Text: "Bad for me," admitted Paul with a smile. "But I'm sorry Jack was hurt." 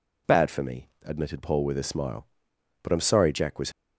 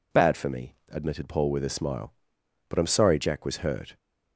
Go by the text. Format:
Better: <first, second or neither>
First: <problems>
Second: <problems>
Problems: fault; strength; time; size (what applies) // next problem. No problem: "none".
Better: second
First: stops before "hurt"; at 3.7 s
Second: none